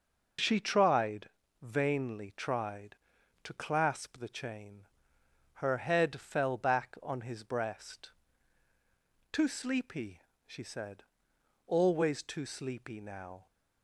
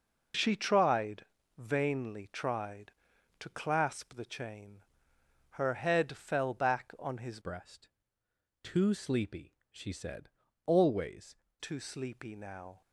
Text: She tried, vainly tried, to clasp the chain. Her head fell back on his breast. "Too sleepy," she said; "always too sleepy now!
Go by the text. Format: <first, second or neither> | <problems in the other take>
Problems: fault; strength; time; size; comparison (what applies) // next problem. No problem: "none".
first | changes voice from "breast" to "always"; from 7.4 to 11.3 s; 3.9 s long